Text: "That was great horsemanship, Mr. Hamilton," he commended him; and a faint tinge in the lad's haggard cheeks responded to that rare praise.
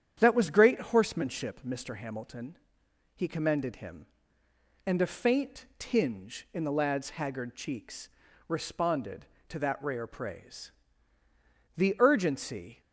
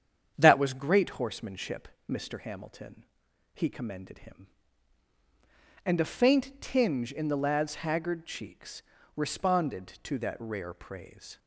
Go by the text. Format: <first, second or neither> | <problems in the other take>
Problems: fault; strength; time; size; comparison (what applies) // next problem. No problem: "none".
second | starts louder than the rest; strong; until 1.1 s; 9 dB; strong in the second // pauses between "cheeks" and "responded"; at 8.0 s; 0.40 s long; slight in the second // goes on to say "The urgency"; noticeable; from 11.7 s on; 1.0 s long